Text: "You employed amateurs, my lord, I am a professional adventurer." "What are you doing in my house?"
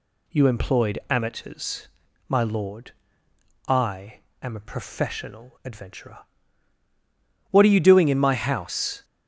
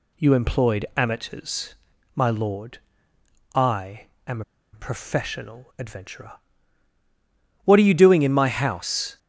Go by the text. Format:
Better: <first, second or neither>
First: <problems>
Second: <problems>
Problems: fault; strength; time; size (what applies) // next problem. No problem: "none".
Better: first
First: pauses between "I" and "am"; slight; at 4.1 s; 0.23 s long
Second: pauses between "I" and "am"; slight; at 4.0 s; 0.22 s long // pauses between "am" and "a"; slight; at 4.4 s; 0.32 s long